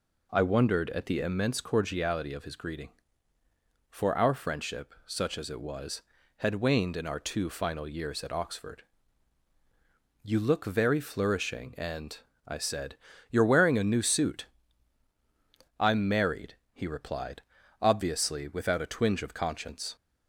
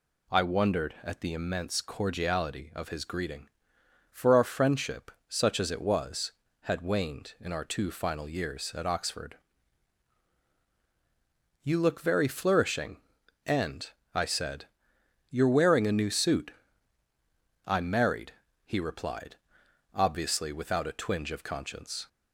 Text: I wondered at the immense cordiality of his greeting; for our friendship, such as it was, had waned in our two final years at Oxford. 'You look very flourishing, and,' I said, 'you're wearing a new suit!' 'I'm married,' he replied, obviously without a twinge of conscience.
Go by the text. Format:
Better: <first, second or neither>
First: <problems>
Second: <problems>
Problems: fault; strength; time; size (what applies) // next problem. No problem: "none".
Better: second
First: starts louder than the rest; until 1.7 s; 3.5 dB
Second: none